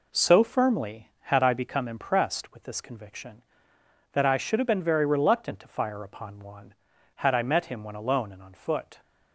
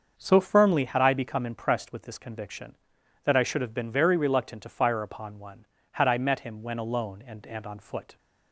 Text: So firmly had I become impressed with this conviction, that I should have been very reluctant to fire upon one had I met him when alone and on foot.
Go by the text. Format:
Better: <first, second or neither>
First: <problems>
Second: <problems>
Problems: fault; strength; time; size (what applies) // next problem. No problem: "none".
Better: first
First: none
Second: starts louder than the rest; until 1.1 s; 6.5 dB // says "and" twice; at 7.4 s